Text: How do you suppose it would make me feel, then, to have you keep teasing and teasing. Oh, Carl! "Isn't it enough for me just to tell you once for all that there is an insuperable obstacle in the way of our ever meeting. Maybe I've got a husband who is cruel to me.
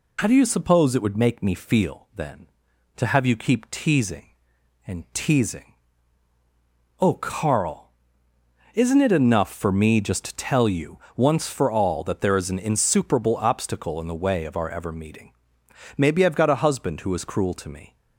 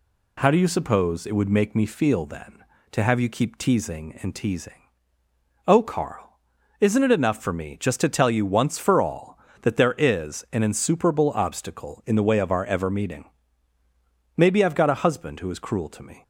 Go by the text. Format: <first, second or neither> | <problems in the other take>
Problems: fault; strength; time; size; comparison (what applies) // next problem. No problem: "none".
second | loses the start of "How"; at 0.1 s; 35 ms // pauses between "you" and "once"; slight; at 10.9 s; 0.18 s long